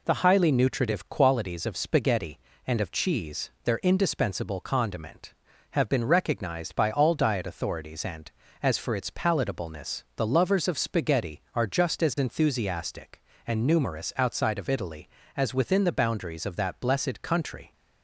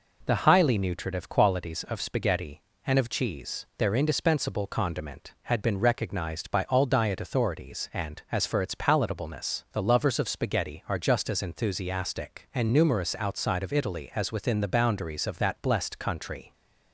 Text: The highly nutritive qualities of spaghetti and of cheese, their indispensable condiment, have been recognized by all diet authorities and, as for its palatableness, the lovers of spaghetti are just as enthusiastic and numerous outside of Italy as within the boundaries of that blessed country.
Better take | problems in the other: first | says "had" for "have"; at 5.4 s

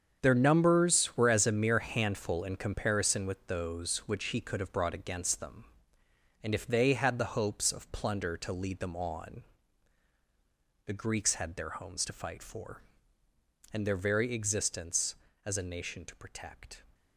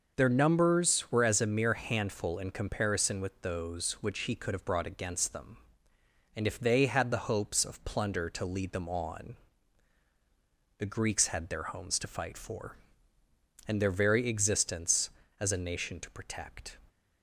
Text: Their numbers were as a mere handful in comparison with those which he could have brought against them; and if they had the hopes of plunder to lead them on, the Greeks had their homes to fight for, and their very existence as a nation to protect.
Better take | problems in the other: second | gets quieter; strong; throughout; 11.5 dB

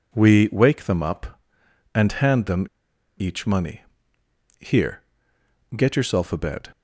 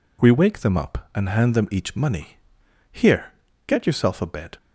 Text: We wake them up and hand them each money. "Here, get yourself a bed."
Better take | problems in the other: second | pauses between "them" and "each"; noticeable; at 2.6 s; 0.54 s long

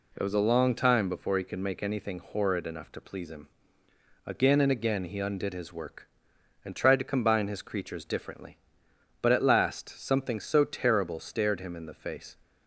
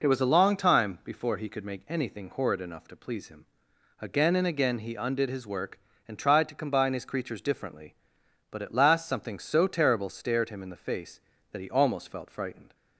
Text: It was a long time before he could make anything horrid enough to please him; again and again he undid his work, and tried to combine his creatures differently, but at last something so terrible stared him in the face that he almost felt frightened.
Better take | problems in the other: second | stops before "that he almost felt frightened"; at 12.4 s

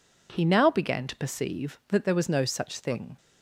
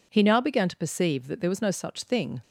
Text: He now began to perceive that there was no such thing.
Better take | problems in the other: neither | none

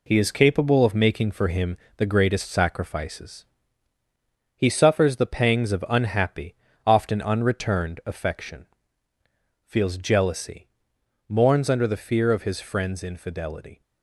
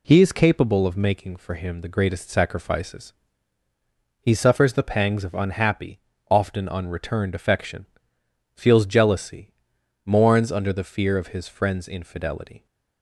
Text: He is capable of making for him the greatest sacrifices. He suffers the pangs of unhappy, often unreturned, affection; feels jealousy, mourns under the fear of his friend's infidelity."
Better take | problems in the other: second | gets quieter; throughout; 7 dB // pauses between "him" and "the"; slight; at 1.7 s; 0.22 s long

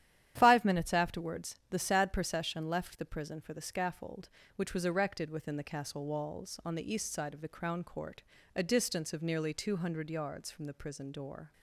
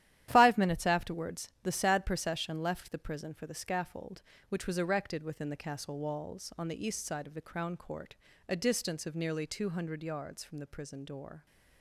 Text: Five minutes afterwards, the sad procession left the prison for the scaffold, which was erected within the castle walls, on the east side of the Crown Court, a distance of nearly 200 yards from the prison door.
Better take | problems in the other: first | gets quieter; strong; throughout; 8.5 dB // starts louder than the rest; strong; until 1.3 s; 12 dB; strong in the first

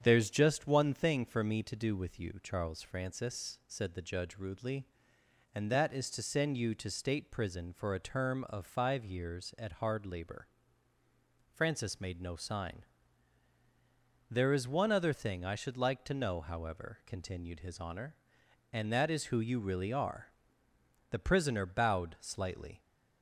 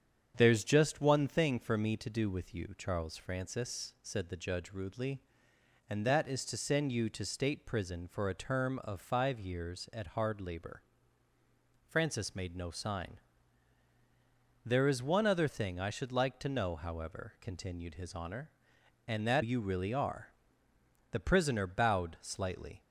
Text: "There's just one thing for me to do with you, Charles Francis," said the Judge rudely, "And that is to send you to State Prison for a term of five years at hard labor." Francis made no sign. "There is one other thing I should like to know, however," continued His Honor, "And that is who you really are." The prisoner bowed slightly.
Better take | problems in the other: first | starts louder than the rest; strong; until 1.3 s; 8 dB; strong in the first // skips "is who"; at 19.4 s

